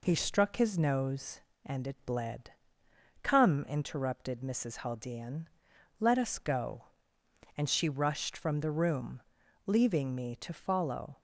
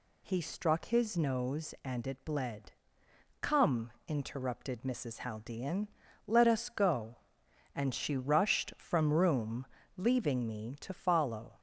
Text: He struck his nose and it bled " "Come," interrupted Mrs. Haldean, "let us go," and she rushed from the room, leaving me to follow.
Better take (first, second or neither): first